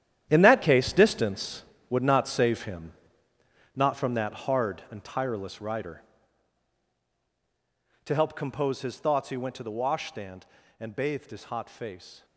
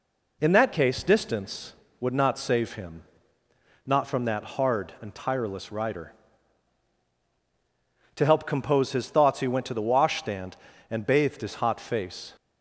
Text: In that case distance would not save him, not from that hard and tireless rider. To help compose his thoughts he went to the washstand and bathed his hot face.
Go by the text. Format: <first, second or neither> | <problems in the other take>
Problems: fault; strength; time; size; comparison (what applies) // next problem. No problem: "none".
second | gets quieter; strong; throughout; 12.5 dB